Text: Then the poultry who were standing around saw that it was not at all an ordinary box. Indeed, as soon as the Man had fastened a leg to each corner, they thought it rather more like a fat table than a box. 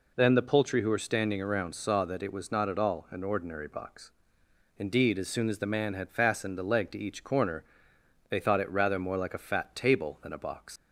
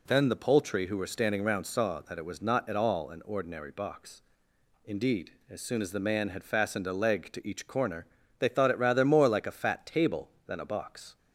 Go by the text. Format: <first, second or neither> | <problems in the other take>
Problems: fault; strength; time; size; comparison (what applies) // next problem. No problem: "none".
second | leaves "box" unfinished; at 10.7 s; 115 ms